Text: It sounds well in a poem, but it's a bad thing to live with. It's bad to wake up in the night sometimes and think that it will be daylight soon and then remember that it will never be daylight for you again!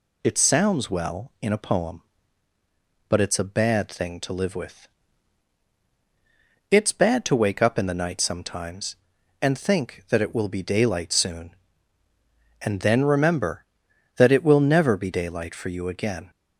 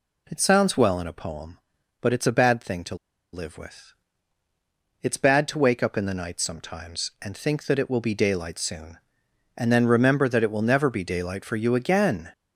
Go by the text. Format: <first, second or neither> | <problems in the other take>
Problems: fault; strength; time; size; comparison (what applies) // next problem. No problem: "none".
first | pauses between "to" and "live"; at 2.9 s; 0.38 s long